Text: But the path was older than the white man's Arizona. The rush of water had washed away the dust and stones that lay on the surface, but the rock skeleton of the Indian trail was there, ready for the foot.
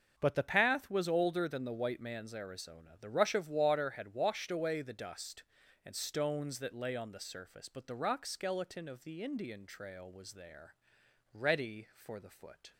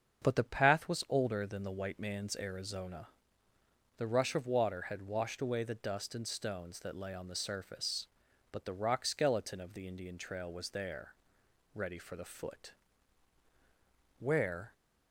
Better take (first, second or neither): first